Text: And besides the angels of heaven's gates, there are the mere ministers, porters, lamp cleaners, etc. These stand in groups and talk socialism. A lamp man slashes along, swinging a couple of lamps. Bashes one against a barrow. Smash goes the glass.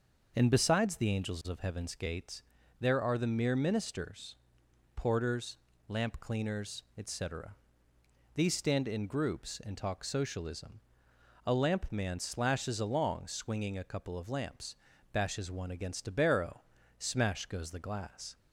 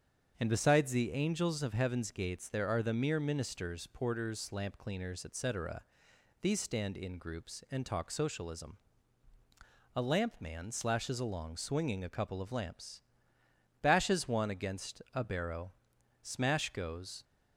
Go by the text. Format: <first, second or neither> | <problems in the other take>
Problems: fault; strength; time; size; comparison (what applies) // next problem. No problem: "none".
first | starts louder than the rest; until 1.4 s; 7 dB; also in the first // stops before "the glass"; at 17.2 s